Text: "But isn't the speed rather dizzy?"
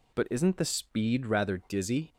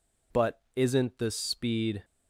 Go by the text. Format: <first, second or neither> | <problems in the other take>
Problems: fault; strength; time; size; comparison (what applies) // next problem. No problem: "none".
first | stops before "rather dizzy"; at 2.0 s